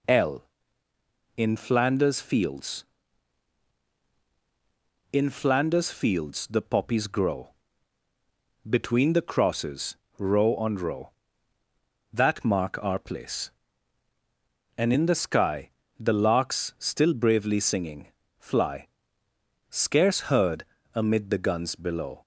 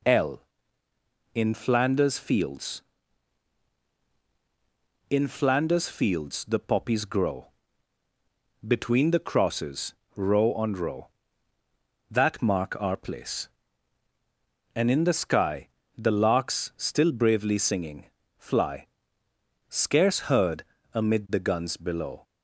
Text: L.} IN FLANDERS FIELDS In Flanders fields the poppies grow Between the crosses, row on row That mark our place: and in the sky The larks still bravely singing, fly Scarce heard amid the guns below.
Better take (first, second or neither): neither